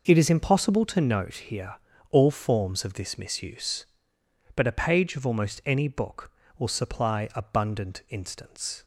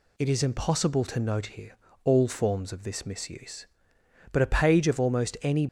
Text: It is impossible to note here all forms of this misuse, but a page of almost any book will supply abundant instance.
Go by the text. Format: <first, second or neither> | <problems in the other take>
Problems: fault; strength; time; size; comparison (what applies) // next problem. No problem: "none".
first | pauses between "here" and "all"; slight; at 1.7 s; 0.28 s long; slight in the first // stops before "book will supply abundant instance"; at 5.6 s